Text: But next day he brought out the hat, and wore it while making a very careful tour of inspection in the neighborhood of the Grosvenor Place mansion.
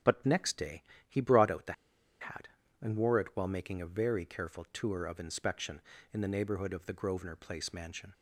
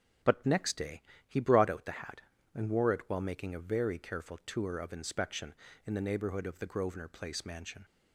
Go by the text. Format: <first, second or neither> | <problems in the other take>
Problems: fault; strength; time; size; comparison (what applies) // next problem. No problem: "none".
second | starts louder than the rest; until 1.2 s; 6.5 dB; also in the second // pauses between "day" and "he"; slight; at 0.8 s; 0.26 s long; slight in the second // pauses between "the" and "hat"; noticeable; at 1.7 s; 0.48 s long